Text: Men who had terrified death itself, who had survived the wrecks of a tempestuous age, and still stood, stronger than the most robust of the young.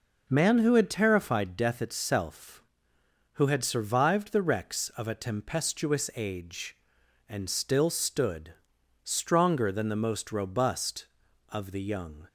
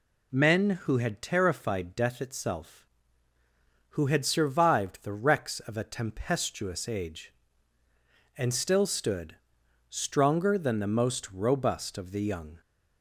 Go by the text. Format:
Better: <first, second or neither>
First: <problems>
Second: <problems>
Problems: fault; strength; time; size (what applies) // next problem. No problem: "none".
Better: second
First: says "Man" for "Men"; at 0.2 s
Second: none